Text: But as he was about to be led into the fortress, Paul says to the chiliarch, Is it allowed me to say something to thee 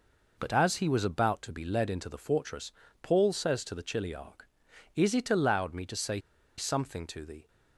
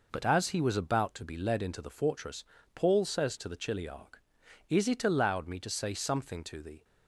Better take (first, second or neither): second